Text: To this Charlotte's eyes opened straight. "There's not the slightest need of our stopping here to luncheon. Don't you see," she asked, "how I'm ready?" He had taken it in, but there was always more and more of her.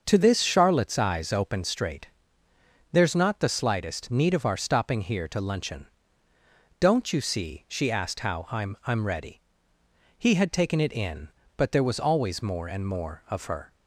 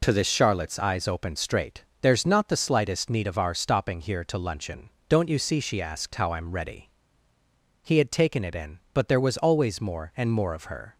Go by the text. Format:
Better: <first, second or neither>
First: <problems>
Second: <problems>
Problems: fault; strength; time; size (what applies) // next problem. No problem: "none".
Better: second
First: starts louder than the rest; until 1.0 s; 6.5 dB // says "I'm" twice; at 8.8 s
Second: none